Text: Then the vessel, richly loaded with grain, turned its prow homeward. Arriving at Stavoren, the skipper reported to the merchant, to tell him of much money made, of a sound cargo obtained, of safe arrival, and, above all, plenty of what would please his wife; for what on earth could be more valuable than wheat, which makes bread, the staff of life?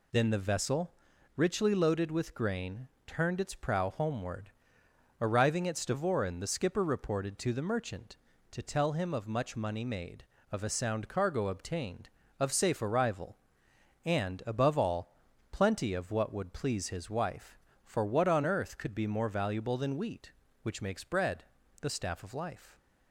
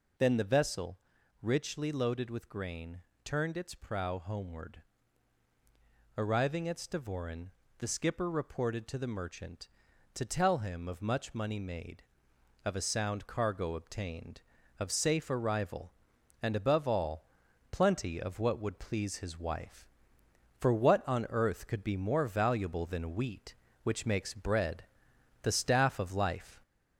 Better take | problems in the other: first | gets louder; slight; throughout; 3 dB

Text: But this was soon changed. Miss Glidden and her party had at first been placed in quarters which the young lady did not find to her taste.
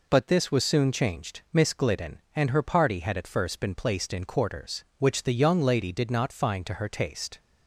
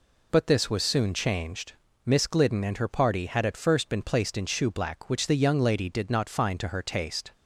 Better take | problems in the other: first | says "shoeblack" for "quarters"; at 4.4 s

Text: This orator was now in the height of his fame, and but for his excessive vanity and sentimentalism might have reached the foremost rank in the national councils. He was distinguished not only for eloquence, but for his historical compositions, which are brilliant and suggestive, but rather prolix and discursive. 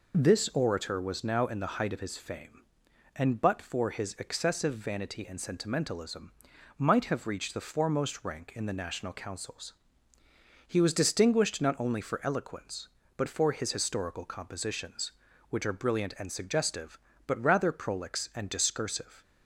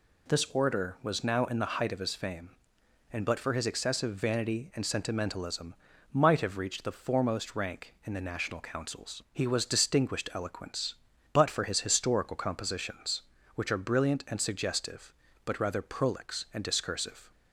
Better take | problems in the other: first | pauses between "sentimentalism" and "might"; at 5.7 s; 0.40 s long; noticeable in the first // skips "not only for"; at 10.3 s

